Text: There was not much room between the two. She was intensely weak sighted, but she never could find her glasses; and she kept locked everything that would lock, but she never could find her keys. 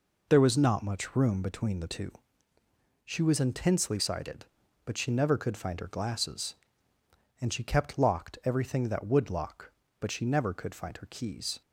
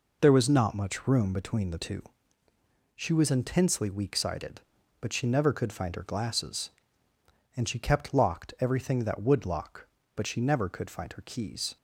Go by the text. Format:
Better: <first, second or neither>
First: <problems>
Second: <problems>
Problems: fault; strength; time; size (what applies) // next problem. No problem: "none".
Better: second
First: skips "weak"; at 3.9 s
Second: none